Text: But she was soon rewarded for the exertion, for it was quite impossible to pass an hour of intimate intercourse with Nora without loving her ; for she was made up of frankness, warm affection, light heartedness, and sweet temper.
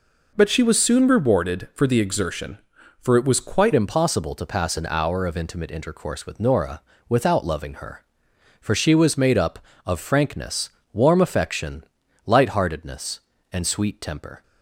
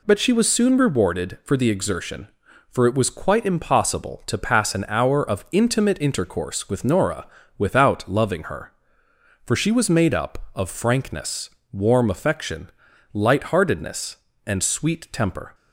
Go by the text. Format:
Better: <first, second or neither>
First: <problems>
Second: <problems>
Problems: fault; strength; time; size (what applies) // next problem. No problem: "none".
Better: second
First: changes voice at "impossible"; from 3.7 s on; 10.7 s long // pauses between "Nora" and "without"; slight; at 6.8 s; 0.28 s long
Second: pauses between "Nora" and "without"; slight; at 7.2 s; 0.32 s long